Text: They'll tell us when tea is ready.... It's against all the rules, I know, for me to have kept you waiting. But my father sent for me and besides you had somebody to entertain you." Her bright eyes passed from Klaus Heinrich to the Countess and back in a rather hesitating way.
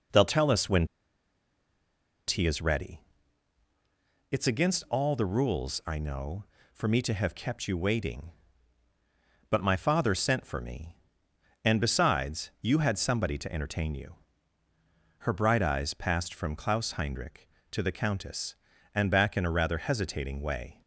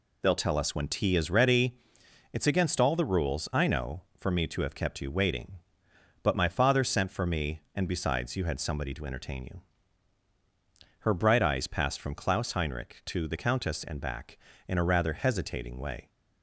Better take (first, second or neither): second